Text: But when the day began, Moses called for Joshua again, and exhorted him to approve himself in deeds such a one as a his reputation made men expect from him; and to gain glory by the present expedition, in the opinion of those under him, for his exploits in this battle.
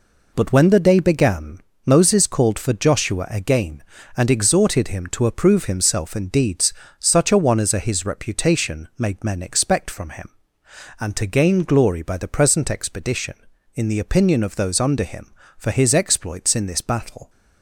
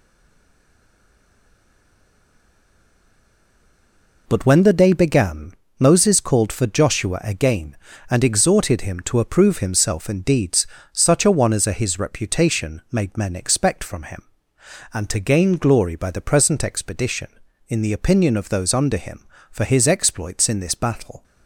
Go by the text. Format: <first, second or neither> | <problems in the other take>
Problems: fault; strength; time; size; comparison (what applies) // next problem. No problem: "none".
first | stays silent before the first word; strong; until 4.2 s; 4.2 s long // pauses between "deeds" and "such"; slight; at 10.6 s; 0.24 s long; slight in the first